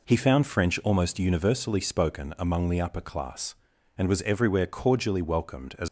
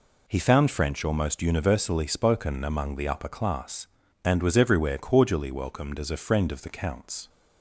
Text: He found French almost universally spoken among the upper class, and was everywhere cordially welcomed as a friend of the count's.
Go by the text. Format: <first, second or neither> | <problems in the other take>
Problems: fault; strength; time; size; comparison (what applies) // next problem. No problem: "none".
second | stops before "a friend of the count's"; at 5.8 s